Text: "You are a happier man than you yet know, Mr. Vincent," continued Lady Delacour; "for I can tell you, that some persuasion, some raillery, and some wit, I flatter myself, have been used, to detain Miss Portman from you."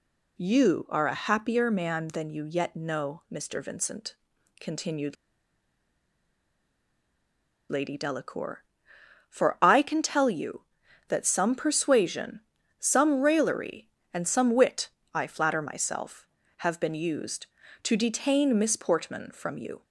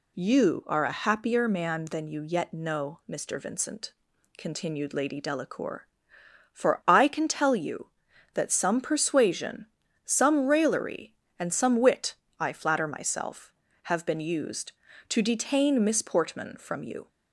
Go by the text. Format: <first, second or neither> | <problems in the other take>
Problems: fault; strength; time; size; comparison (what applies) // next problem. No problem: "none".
second | pauses between "continued" and "Lady"; strong; at 5.1 s; 2.5 s long